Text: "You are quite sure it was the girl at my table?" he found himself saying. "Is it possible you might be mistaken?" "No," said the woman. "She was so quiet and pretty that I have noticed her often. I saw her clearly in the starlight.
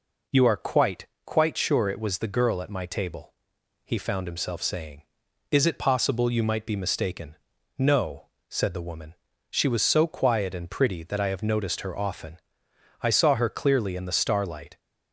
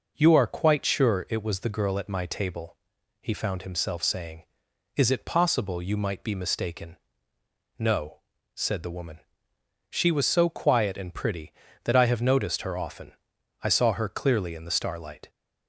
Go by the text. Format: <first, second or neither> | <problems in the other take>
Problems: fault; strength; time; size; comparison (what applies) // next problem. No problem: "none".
second | says "quite" twice; at 1.2 s